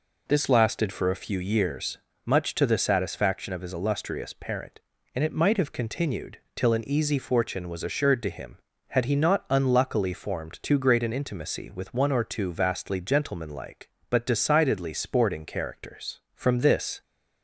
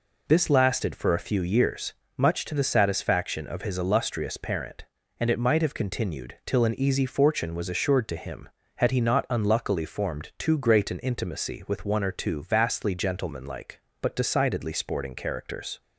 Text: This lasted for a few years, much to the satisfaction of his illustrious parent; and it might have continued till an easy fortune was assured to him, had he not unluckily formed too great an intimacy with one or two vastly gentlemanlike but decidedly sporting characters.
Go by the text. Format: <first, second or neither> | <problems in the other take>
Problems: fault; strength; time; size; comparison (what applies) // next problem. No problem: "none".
second | pauses between "continued" and "till"; slight; at 6.3 s; 0.16 s long // goes on to say "From this"; noticeable; from 16.3 s on; 0.68 s long